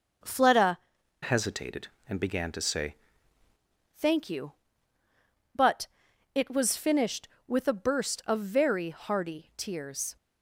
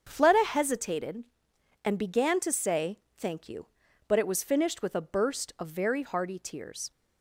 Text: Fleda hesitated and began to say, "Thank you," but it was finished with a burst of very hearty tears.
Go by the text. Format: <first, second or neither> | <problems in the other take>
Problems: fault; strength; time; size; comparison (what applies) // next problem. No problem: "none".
second | starts louder than the rest; noticeable; until 1.6 s; 6 dB; strong in the second // changes voice from "hesitated" to "say"; from 1.2 to 2.9 s; 1.7 s long // pauses between "but" and "it"; noticeable; at 5.8 s; 0.48 s long